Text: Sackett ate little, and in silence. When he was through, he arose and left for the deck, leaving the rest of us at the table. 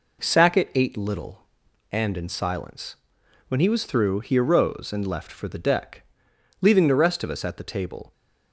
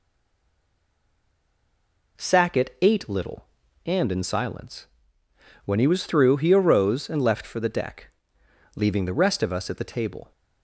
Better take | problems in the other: first | stays silent before the first word; until 2.1 s; 2.1 s long

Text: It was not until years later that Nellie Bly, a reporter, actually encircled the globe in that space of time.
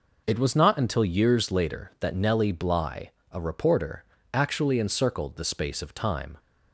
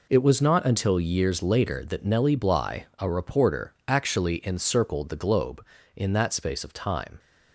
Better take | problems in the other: second | skips "globe in that"; at 5.4 s

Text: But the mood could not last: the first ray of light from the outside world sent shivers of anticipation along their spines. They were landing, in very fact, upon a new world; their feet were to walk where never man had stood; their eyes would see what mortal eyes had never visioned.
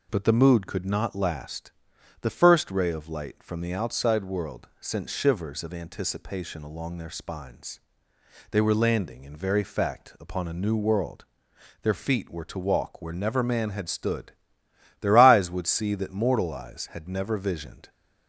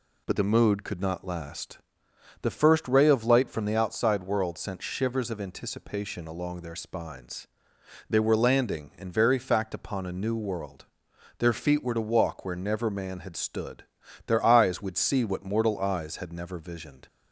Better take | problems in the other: second | says "that" for "what"; at 15.9 s

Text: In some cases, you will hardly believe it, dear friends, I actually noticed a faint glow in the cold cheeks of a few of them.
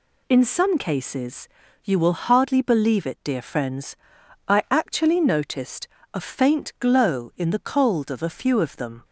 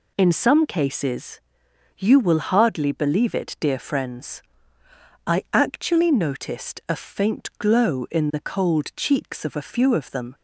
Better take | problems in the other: second | pauses between "noticed" and "a"; slight; at 5.8 s; 0.28 s long // skips "cheeks"; at 8.0 s

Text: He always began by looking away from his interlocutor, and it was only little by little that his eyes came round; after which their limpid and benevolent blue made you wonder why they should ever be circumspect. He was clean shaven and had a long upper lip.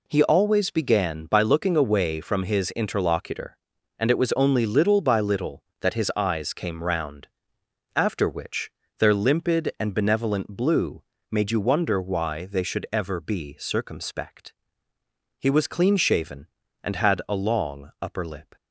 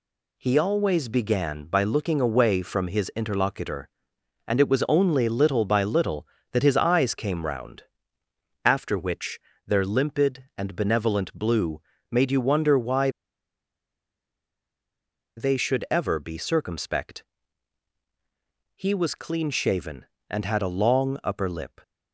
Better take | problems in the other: first | pauses between "which" and "their"; slight; at 9.3 s; 0.26 s long; slight in the first // pauses between "blue" and "made"; slight; at 11.8 s; 0.30 s long; slight in the first // pauses between "why" and "they"; strong; at 13.0 s; 2.2 s long

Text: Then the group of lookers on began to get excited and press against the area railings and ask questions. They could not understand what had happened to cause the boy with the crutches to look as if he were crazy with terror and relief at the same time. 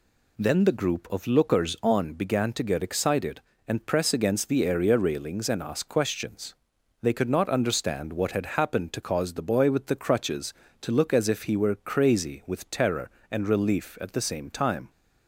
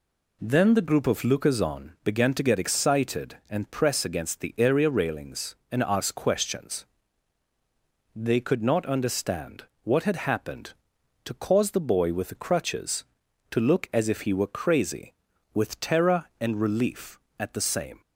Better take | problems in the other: first | pauses between "understand" and "what"; slight; at 9.6 s; 0.18 s long // stops before "time"; at 18.0 s

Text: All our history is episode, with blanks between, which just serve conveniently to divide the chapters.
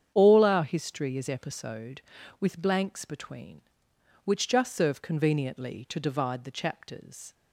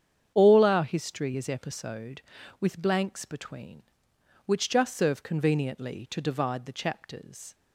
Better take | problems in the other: neither | starts louder than the rest; strong; the same in both

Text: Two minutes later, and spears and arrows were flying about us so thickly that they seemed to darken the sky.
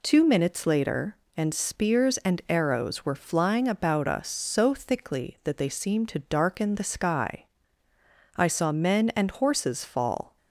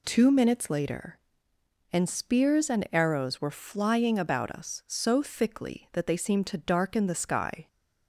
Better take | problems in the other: second | goes on to say "I saw men and horses fall"; strong; from 8.3 s on; 2.0 s long

